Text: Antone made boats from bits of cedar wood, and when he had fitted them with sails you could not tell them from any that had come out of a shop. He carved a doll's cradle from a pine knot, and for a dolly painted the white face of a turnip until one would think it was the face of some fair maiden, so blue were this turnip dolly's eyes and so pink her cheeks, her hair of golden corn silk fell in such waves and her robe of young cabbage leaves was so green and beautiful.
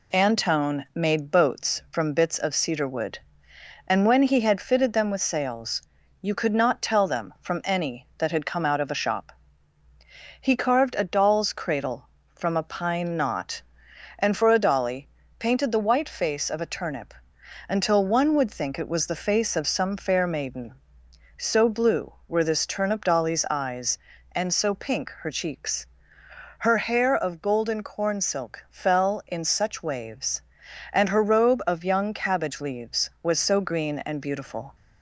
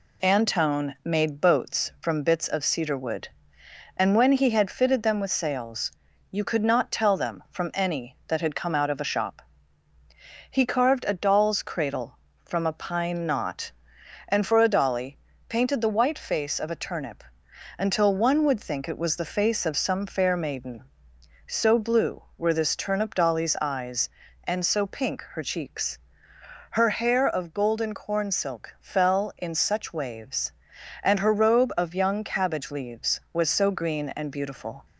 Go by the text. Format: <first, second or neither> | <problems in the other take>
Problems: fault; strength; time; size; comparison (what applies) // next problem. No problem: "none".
neither | pauses between "sails" and "you"; the same in both // pauses between "dolly" and "painted"; slight; the same in both // pauses between "turnip" and "until"; noticeable; the same in both